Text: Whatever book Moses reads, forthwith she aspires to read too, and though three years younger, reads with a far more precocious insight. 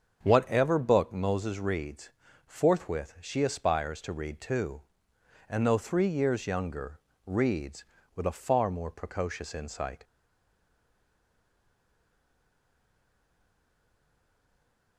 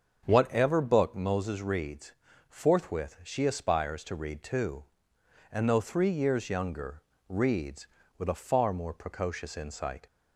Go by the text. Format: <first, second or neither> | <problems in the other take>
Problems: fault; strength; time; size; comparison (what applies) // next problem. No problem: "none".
second | starts louder than the rest; until 1.2 s; 7 dB; also in the second // stays silent after the last word; strong; from 10.0 s on; 4.9 s long